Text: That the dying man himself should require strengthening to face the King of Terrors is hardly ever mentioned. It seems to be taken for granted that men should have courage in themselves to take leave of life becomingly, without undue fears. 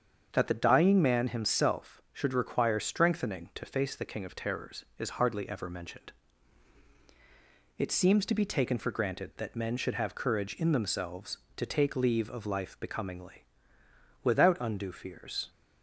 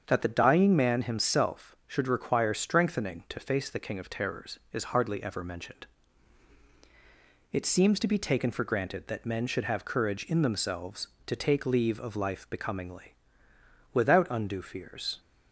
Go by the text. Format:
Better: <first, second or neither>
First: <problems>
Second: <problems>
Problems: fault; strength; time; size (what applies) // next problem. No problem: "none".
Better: neither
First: starts louder than the rest; strong; until 1.3 s; 7 dB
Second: starts louder than the rest; strong; until 1.0 s; 7.5 dB